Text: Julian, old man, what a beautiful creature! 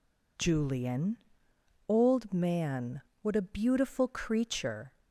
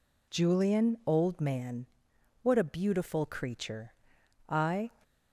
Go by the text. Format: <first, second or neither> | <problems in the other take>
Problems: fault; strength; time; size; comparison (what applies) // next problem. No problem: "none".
first | goes on to say "I"; slight; from 4.4 s on; 0.40 s long